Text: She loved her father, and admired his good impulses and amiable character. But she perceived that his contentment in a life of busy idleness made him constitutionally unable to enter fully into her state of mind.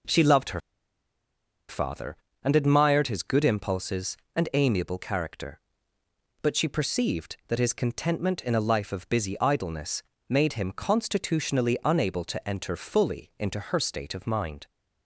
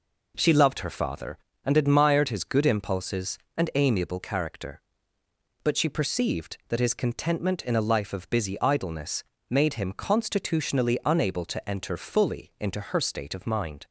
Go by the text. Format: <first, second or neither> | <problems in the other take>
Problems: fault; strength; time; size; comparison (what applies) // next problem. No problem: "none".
second | pauses between "her" and "father"; at 0.5 s; 1.0 s long // pauses between "idleness" and "made"; slight; at 10.0 s; 0.26 s long; slight in the second